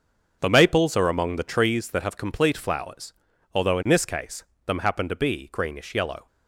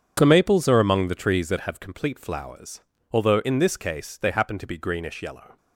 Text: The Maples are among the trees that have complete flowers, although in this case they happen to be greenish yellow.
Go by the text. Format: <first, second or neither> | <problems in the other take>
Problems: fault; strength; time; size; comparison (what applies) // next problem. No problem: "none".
second | starts louder than the rest; until 1.4 s; 6.5 dB // says "them" for "they"; at 4.6 s